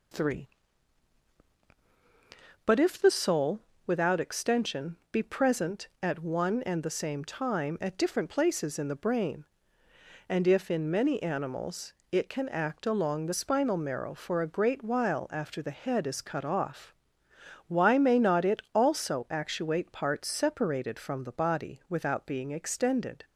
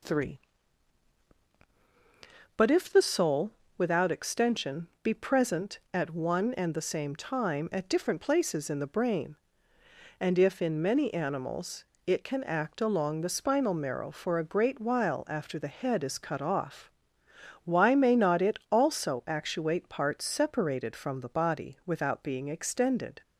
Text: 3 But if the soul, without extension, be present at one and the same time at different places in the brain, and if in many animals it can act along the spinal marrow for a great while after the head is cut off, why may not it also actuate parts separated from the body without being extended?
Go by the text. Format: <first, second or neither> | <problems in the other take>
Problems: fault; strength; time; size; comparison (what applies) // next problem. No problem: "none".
neither | pauses between "animals" and "it"; slight; the same in both